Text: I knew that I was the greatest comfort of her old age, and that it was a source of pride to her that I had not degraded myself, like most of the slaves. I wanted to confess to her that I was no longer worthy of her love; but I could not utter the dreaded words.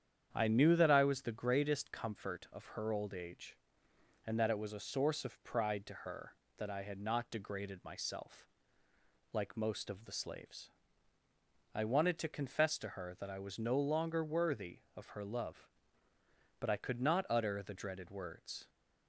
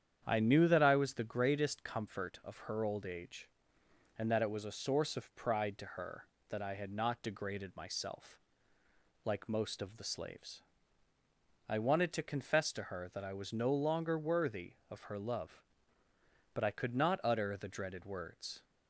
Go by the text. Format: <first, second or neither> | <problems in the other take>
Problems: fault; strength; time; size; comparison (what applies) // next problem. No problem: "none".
neither | starts louder than the rest; strong; the same in both